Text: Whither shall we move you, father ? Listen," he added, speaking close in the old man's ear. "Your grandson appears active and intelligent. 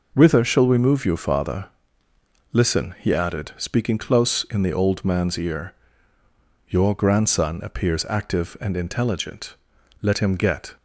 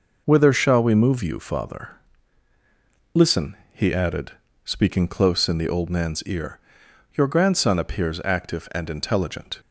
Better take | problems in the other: second | goes on to say "Let him get"; noticeable; from 10.0 s on; 0.74 s long

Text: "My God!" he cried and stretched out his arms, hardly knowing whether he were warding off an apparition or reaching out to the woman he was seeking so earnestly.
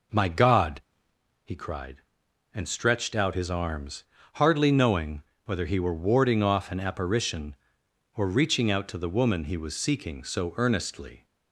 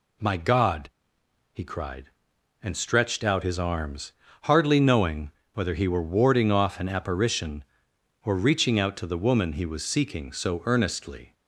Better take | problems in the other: second | starts louder than the rest; noticeable; until 1.2 s; 5 dB // pauses between "knowing" and "whether"; slight; at 5.2 s; 0.24 s long; slight in the second

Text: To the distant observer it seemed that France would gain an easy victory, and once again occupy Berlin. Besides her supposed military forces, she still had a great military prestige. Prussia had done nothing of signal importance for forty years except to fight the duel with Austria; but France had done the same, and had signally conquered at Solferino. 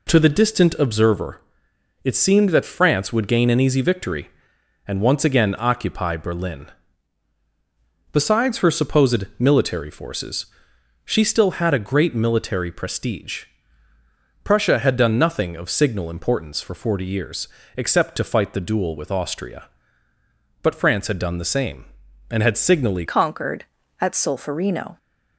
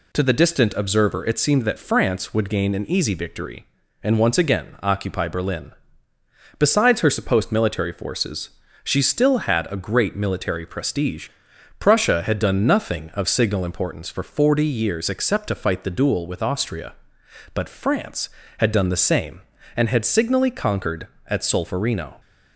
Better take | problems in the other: second | pauses between "observer" and "it"; noticeable; at 1.4 s; 0.60 s long // pauses between "years" and "except"; slight; at 17.4 s; 0.28 s long // changes voice at "conquered"; from 23.0 s on; 1.9 s long

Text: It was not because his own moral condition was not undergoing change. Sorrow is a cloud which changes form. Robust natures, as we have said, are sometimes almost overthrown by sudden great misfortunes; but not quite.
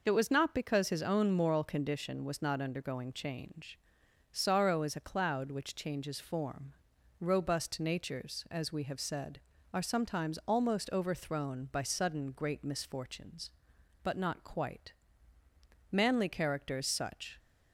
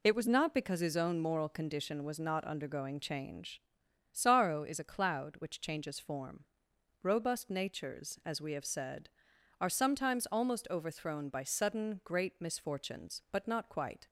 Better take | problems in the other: second | goes on to say "Manly characters such"; from 15.9 s on; 1.4 s long

